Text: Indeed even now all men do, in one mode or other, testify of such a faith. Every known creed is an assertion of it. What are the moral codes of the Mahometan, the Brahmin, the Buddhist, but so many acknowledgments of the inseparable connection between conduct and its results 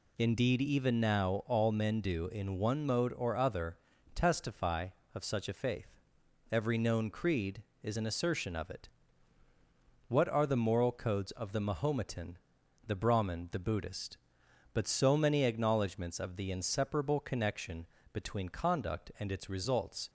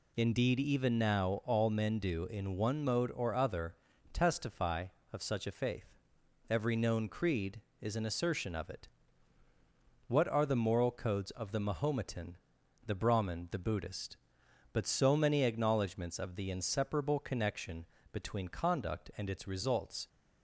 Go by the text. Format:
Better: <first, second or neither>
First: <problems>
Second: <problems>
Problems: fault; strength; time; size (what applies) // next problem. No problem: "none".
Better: neither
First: pauses between "connection" and "between"; slight; at 17.8 s; 0.26 s long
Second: pauses between "connection" and "between"; slight; at 17.8 s; 0.26 s long